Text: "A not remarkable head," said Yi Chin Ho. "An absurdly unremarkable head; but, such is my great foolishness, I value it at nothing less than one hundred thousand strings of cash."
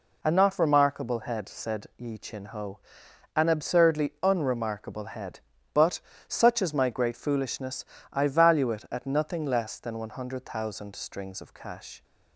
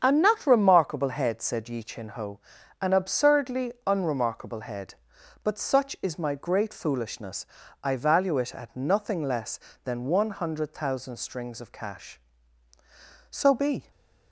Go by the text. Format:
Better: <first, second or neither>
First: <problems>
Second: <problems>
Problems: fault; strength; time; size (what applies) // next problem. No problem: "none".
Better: first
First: none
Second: starts louder than the rest; strong; until 1.0 s; 7.5 dB // goes on to say "So be"; from 13.3 s on; 0.60 s long